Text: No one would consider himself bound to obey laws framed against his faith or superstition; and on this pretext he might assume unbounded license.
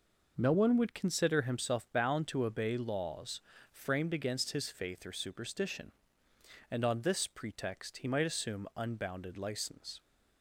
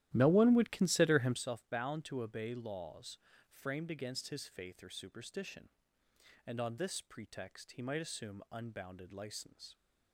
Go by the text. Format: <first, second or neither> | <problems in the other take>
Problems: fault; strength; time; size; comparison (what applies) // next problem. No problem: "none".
first | starts louder than the rest; strong; until 1.4 s; 13.5 dB // pauses between "laws" and "framed"; slight; at 3.1 s; 0.34 s long; slight in the first